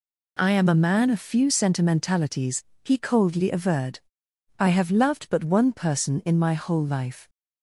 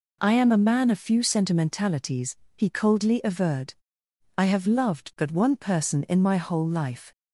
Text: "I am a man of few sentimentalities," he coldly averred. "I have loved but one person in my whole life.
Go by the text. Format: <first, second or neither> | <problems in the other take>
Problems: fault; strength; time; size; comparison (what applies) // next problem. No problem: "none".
neither | none